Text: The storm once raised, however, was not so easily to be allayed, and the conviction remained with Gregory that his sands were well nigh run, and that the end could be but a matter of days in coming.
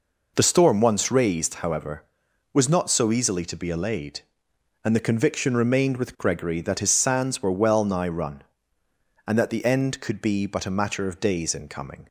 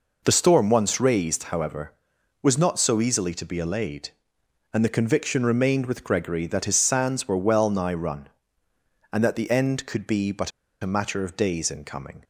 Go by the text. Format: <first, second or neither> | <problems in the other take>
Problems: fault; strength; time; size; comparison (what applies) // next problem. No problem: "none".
first | pauses between "but" and "a"; slight; at 10.5 s; 0.32 s long